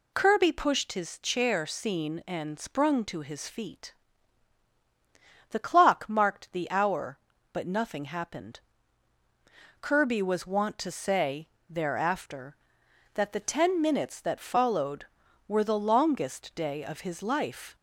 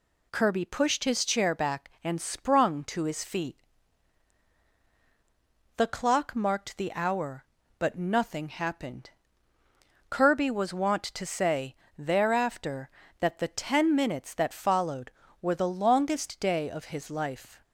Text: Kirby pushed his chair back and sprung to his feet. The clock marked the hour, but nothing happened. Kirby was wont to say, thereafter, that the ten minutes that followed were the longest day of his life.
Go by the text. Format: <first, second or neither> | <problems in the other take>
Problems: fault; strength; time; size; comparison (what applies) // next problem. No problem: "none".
second | says "seen" for "back"; at 1.6 s